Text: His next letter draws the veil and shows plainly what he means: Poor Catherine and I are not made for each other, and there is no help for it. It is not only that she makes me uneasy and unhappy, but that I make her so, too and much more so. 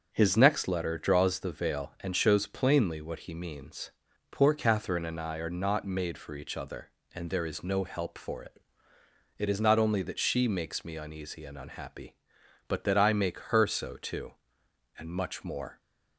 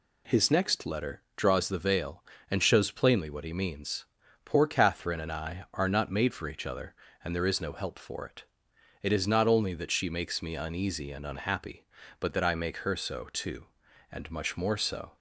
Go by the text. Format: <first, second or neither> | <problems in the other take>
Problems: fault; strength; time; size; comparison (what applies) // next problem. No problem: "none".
second | starts louder than the rest; until 1.1 s; 7 dB // stops before "so"; at 15.7 s